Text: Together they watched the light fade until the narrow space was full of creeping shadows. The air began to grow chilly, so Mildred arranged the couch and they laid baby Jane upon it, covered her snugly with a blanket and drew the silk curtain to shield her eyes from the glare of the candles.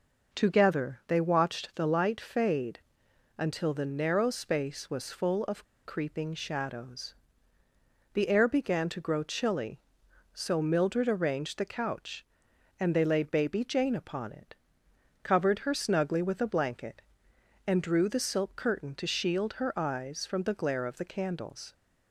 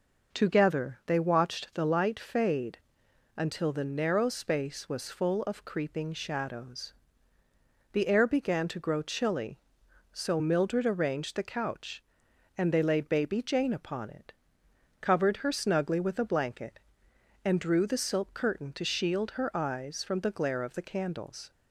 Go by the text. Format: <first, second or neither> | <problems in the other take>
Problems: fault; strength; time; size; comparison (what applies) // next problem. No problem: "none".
second | pauses between "fade" and "until"; noticeable; at 2.7 s; 0.58 s long; noticeable in the second // pauses between "of" and "creeping"; slight; at 5.6 s; 0.20 s long